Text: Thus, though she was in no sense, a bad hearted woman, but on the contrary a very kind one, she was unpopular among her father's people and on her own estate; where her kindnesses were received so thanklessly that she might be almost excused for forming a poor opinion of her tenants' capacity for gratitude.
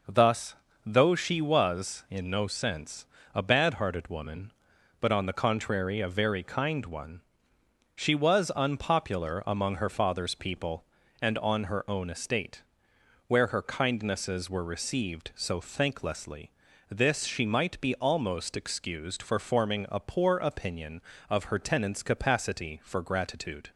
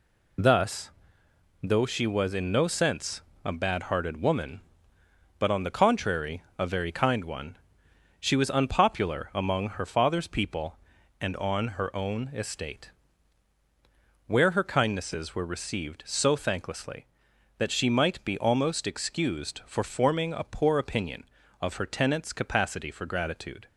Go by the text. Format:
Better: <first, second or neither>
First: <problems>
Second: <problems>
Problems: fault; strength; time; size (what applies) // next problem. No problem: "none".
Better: second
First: says "this" for "that"; at 16.8 s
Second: none